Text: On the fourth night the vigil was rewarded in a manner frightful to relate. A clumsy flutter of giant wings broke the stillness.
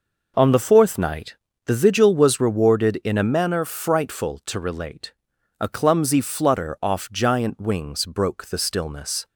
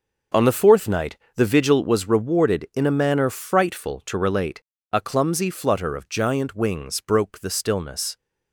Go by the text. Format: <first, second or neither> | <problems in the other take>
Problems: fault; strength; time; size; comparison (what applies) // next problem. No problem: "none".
second | pauses between "night" and "the"; slight; at 1.3 s; 0.30 s long; slight in the second // says "off" for "of"; at 6.8 s